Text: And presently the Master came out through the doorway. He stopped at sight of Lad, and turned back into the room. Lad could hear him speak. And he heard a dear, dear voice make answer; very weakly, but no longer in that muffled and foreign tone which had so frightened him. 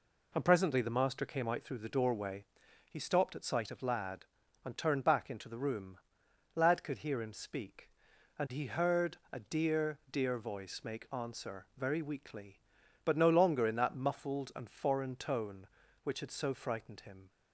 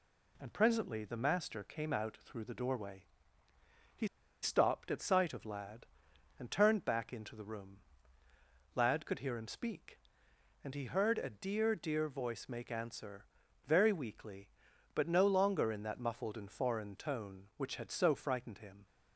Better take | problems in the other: first | pauses between "He" and "stopped"; at 4.0 s; 0.36 s long

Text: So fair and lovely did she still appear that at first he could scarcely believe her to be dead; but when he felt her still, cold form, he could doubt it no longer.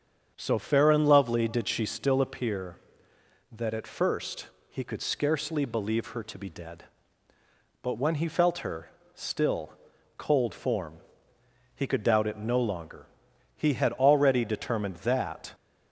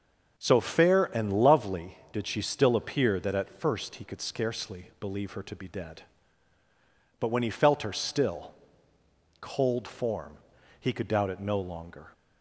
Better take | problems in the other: second | starts louder than the rest; strong; until 1.3 s; 7.5 dB; also in the second // pauses between "first" and "he"; slight; at 4.4 s; 0.20 s long // pauses between "her" and "still"; slight; at 8.8 s; 0.26 s long // goes on to say "He had already determined that"; strong; from 13.5 s on; 1.9 s long

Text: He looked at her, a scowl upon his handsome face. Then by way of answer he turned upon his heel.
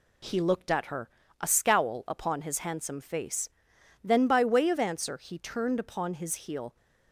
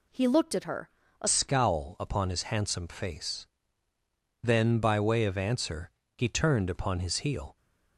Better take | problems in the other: first | changes voice at "scowl"; from 1.2 s on; 6.3 s long // pauses between "answer" and "he"; slight; at 5.8 s; 0.26 s long

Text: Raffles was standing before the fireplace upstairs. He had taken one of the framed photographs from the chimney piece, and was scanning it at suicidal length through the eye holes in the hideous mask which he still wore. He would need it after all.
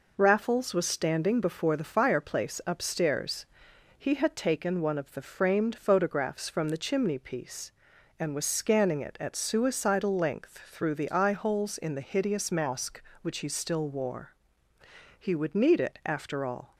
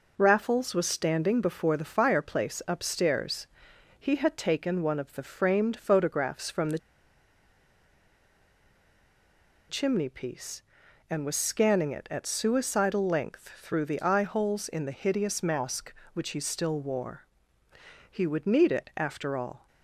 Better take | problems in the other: first | pauses between "the" and "chimney"; strong; at 6.7 s; 2.9 s long

